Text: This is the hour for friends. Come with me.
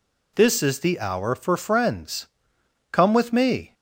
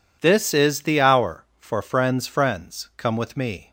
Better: first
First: none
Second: says "friends" twice; at 2.2 s

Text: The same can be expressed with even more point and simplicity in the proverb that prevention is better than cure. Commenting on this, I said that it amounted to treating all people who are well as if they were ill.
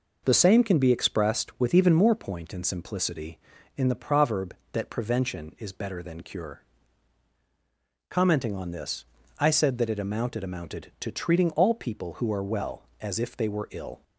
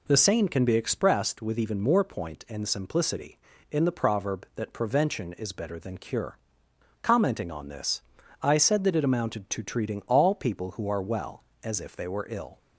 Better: second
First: says "amounted" twice; at 10.4 s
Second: none

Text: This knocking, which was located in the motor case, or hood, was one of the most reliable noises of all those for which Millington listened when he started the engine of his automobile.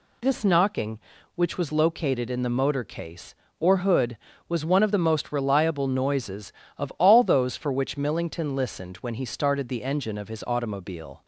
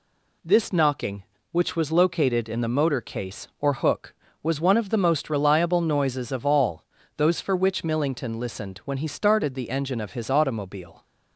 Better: first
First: none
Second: says "hook" for "hood"; at 3.7 s // pauses between "all" and "those"; slight; at 6.8 s; 0.32 s long

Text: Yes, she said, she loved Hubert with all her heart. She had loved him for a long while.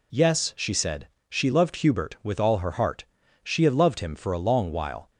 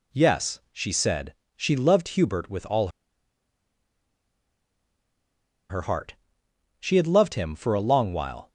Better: first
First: none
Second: pauses between "all" and "her"; strong; at 2.8 s; 2.8 s long

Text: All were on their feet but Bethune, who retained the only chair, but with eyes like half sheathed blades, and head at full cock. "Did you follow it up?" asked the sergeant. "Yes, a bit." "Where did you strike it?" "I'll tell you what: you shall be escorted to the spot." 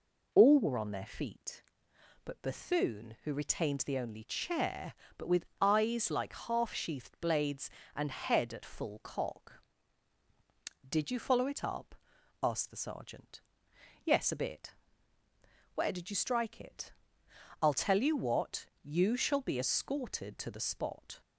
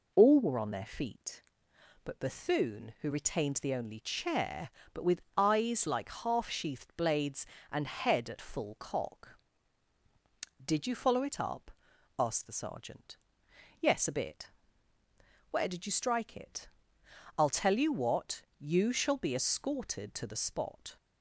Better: neither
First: pauses between "with" and "eyes"; slight; at 5.4 s; 0.16 s long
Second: pauses between "with" and "eyes"; slight; at 5.2 s; 0.16 s long

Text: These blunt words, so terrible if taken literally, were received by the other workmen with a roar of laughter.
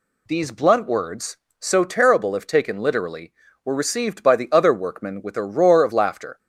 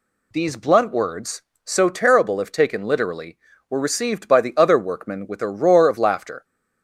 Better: neither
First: none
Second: none

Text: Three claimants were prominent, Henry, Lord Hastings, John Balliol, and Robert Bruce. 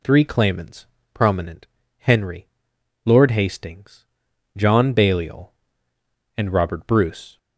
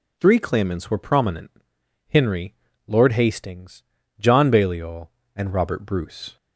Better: second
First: skips "were"; at 0.9 s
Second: none

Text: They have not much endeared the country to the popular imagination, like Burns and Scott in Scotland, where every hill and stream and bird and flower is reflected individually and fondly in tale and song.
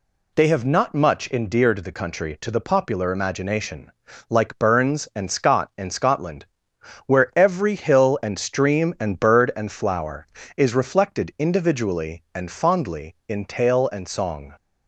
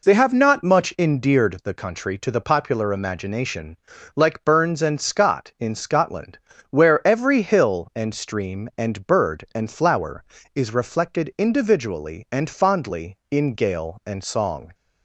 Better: first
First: none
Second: says "gale" for "tale"; at 13.5 s

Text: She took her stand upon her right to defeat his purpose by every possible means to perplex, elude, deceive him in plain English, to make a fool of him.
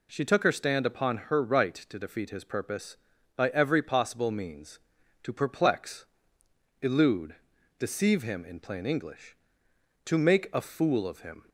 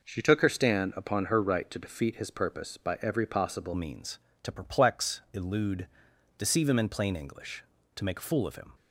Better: first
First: none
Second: changes voice at "means"; from 3.7 s on; 5.0 s long

